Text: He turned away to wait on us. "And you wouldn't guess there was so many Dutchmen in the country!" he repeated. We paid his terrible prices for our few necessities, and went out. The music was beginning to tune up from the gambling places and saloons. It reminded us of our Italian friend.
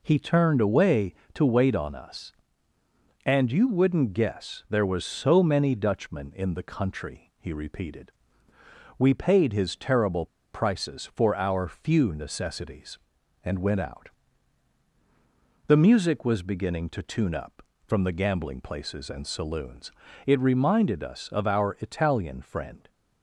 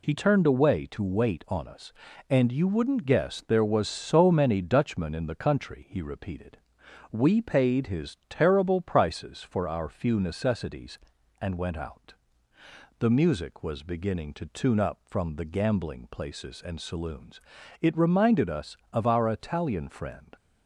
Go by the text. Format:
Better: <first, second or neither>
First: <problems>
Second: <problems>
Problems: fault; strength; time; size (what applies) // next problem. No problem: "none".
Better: second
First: pauses between "terrible" and "prices"; slight; at 10.2 s; 0.26 s long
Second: none